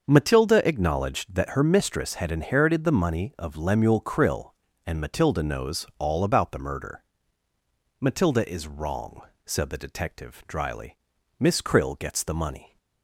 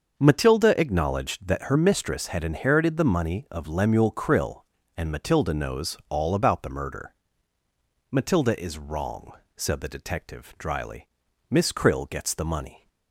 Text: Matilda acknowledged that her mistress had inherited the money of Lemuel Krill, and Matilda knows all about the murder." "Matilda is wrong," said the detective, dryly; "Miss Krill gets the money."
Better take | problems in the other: neither | starts louder than the rest; the same in both

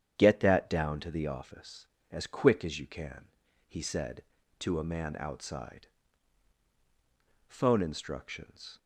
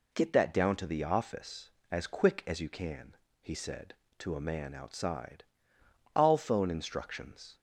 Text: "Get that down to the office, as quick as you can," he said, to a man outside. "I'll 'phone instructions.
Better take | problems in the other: second | starts louder than the rest; strong; until 1.2 s; 8.5 dB // skips "I'll"; at 6.6 s

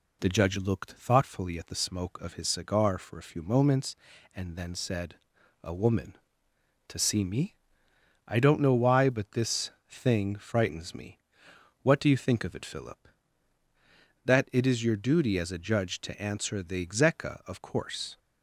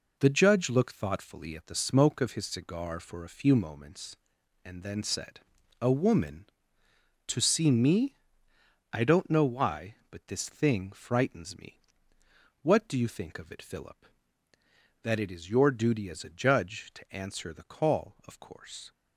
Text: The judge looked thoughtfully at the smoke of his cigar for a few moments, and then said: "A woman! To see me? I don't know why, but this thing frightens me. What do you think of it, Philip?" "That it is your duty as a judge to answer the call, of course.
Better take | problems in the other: second | pauses between "this" and "thing"; slight; at 9.7 s; 0.18 s long // says "execa" for "call"; at 16.8 s

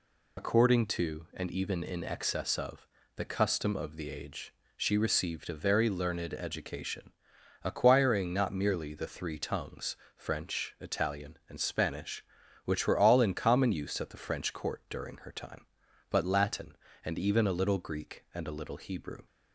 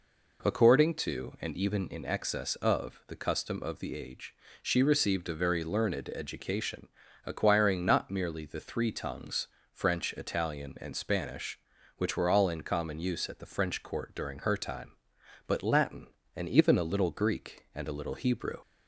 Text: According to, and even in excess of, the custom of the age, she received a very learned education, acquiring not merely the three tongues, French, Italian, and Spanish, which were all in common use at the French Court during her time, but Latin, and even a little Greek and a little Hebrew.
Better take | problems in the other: second | loses the start of "According"; at 0.3 s; 75 ms

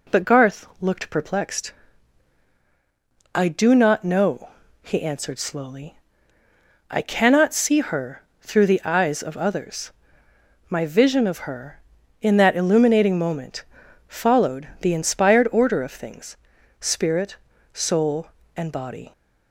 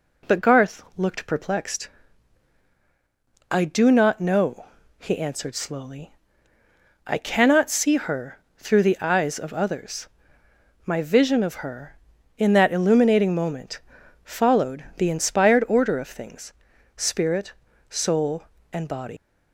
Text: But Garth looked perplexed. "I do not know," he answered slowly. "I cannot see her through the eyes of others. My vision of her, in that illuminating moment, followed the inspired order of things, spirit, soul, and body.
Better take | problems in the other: first | pauses between "her" and "through"; slight; at 8.3 s; 0.18 s long; slight in the first // leaves "body" unfinished; at 19.1 s; 115 ms

